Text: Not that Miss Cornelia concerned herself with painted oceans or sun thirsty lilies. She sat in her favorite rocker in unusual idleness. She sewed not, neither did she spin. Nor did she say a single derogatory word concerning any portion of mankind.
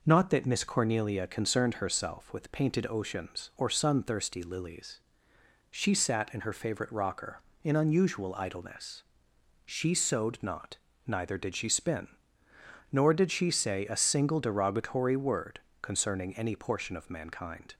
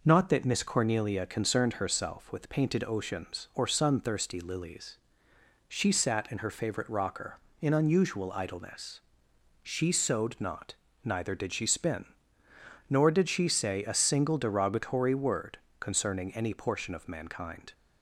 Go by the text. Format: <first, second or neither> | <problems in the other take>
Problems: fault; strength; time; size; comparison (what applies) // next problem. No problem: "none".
neither | pauses between "word" and "concerning"; slight; the same in both